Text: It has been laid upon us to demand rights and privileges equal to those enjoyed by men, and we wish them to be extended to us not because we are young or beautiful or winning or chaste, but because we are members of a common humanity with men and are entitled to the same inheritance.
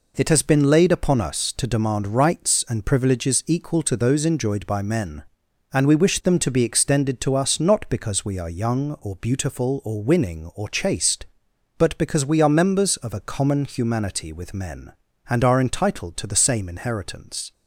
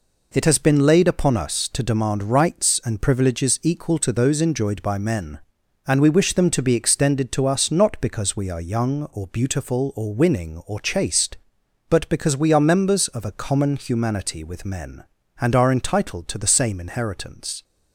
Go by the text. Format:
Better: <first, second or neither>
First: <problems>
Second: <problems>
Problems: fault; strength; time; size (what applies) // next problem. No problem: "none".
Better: neither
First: none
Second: none